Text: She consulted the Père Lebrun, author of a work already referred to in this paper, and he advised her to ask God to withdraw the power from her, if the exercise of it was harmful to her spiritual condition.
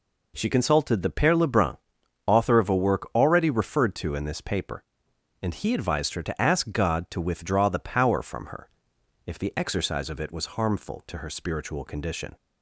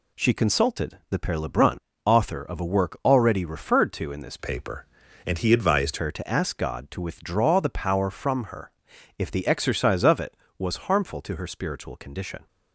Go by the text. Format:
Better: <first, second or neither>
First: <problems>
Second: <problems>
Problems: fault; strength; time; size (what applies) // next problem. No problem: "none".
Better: first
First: none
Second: changes voice from "paper" to "advised"; from 4.3 to 5.9 s; 1.6 s long